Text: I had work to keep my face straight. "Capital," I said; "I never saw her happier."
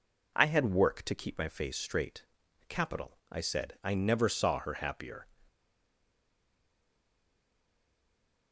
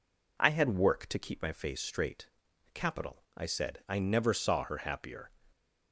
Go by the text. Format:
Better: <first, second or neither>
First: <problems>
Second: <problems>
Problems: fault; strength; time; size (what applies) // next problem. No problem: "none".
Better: second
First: stays silent after the last word; strong; from 5.4 s on; 3.1 s long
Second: none